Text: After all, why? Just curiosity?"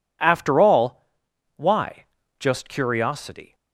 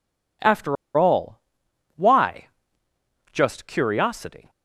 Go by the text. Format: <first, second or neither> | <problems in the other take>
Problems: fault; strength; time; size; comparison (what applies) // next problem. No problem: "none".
first | pauses between "After" and "all"; slight; at 0.7 s; 0.22 s long